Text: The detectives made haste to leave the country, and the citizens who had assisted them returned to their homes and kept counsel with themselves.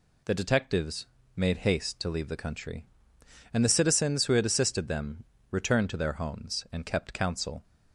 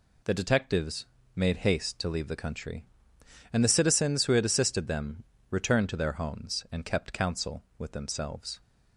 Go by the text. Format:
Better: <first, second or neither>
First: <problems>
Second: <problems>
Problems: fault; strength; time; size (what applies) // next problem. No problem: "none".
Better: second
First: pauses between "detectives" and "made"; slight; at 1.0 s; 0.30 s long // pauses between "them" and "returned"; slight; at 5.2 s; 0.26 s long // stops before "with themselves"; at 7.6 s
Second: pauses between "detectives" and "made"; slight; at 1.0 s; 0.30 s long // pauses between "them" and "returned"; slight; at 5.2 s; 0.26 s long